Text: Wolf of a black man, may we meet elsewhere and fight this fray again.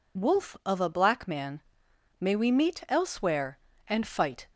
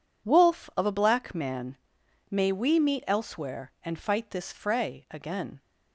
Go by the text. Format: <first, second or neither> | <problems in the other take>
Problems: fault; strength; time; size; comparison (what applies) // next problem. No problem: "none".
second | stops before "this fray again"; at 4.5 s